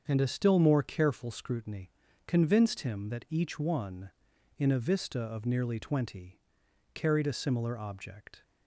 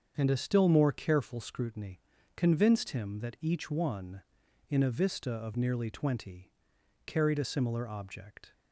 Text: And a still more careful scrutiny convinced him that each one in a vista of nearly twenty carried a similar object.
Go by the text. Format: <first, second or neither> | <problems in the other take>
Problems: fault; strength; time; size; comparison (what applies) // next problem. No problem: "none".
neither | starts louder than the rest; strong; the same in both // pauses between "scrutiny" and "convinced"; the same in both // pauses between "twenty" and "carried"; noticeable; the same in both